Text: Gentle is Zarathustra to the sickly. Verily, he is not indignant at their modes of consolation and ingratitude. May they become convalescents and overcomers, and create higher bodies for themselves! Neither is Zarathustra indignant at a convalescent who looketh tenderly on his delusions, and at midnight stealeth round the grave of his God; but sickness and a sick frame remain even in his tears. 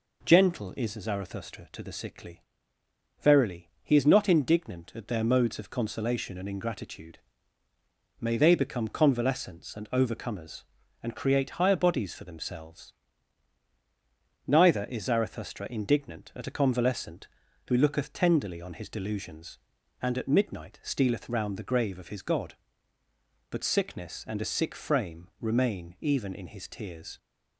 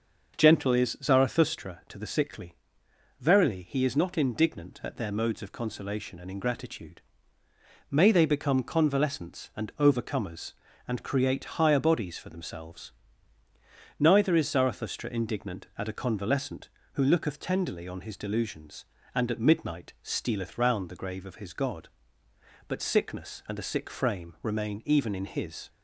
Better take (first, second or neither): first